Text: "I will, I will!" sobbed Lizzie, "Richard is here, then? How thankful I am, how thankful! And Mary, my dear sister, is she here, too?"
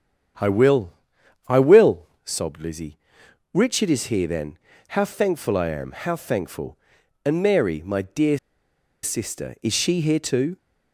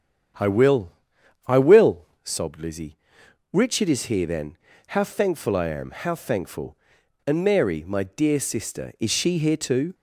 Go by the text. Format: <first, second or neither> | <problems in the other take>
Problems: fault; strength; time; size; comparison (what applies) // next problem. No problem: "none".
second | starts louder than the rest; strong; until 1.9 s; 8.5 dB; strong in the second // pauses between "dear" and "sister"; noticeable; at 8.3 s; 0.66 s long